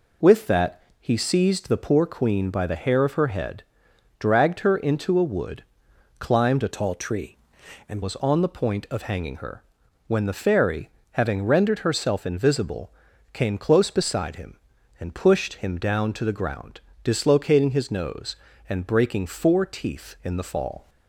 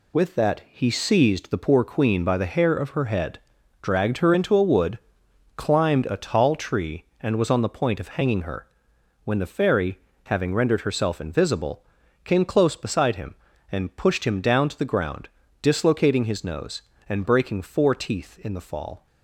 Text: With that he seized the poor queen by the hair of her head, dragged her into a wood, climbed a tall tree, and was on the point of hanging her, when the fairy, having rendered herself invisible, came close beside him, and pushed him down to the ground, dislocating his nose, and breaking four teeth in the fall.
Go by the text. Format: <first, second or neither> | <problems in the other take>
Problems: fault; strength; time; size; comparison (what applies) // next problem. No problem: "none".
second | pauses between "that" and "he"; slight; at 0.7 s; 0.20 s long // changes voice from "tall" to "and"; from 6.7 to 8.0 s; 1.3 s long